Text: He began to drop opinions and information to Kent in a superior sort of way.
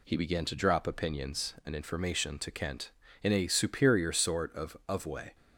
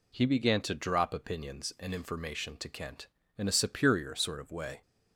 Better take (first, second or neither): second